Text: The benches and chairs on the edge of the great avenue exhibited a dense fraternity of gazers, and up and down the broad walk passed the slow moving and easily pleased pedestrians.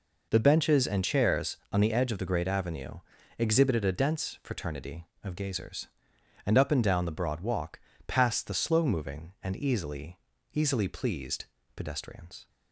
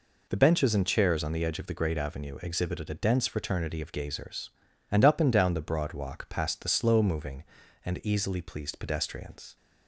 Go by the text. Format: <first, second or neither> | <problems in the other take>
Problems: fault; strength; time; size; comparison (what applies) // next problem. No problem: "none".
second | pauses between "avenue" and "exhibited"; at 3.0 s; 0.38 s long // pauses between "walk" and "passed"; slight; at 7.8 s; 0.26 s long // says "easily" twice; at 10.5 s // pauses between "pleased" and "pedestrians"; slight; at 11.4 s; 0.32 s long